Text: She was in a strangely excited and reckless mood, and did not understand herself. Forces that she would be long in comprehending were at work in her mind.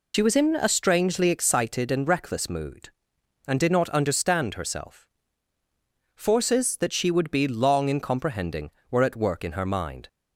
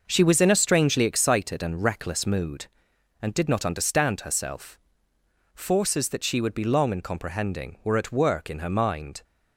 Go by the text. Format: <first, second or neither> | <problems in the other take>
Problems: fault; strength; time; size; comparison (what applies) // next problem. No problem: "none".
second | loses the start of "She"; at 0.1 s; 60 ms